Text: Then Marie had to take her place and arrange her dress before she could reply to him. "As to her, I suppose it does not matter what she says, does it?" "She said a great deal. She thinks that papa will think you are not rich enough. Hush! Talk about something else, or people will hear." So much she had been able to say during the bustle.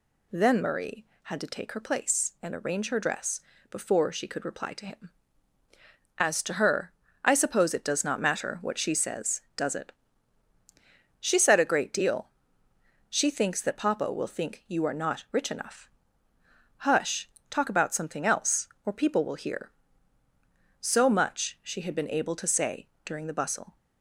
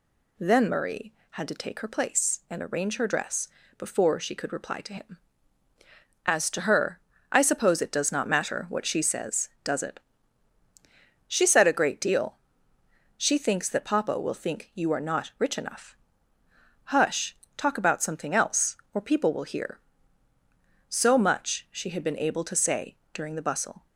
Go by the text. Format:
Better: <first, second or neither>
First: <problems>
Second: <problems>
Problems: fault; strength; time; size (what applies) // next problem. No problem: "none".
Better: neither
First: pauses between "dress" and "before"; slight; at 3.4 s; 0.30 s long // pauses between "say" and "during"; slight; at 22.8 s; 0.16 s long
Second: pauses between "dress" and "before"; slight; at 3.4 s; 0.30 s long // pauses between "say" and "during"; slight; at 22.9 s; 0.16 s long